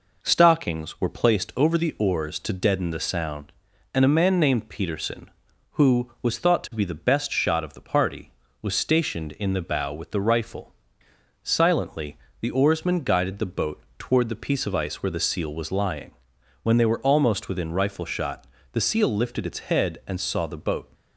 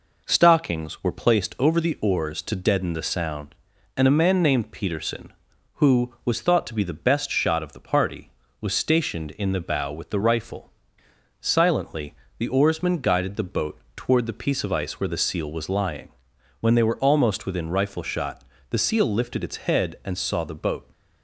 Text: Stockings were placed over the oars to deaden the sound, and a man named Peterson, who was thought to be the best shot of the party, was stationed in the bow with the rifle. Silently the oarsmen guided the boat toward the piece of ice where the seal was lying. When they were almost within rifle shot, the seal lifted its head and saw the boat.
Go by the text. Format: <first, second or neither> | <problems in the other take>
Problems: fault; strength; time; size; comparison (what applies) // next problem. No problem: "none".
neither | pauses between "Silently" and "the"; slight; the same in both // pauses between "boat" and "toward"; slight; the same in both